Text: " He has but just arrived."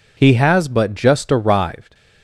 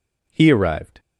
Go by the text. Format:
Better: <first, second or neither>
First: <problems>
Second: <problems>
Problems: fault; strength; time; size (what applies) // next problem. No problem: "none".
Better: first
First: none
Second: skips "has but just"; at 0.5 s